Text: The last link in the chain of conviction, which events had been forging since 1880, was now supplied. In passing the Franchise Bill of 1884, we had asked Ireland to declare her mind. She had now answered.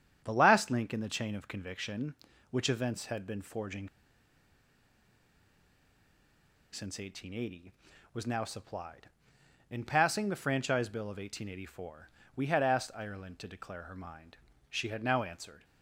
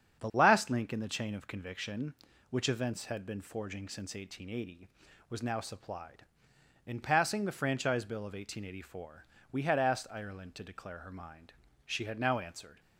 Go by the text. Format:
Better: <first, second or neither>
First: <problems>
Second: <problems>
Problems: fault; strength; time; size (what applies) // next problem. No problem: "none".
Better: second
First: starts louder than the rest; strong; until 1.2 s; 8 dB // pauses between "forging" and "since"; strong; at 3.8 s; 2.8 s long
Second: starts louder than the rest; strong; until 1.2 s; 8 dB